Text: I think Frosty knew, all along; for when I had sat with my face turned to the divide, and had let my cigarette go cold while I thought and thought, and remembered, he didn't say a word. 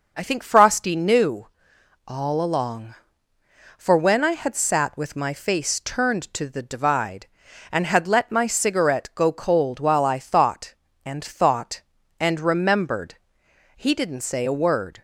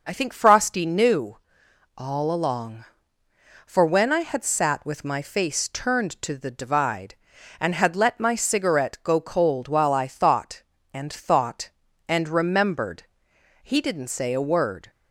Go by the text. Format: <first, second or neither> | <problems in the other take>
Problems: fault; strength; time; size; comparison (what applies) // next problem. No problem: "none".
neither | none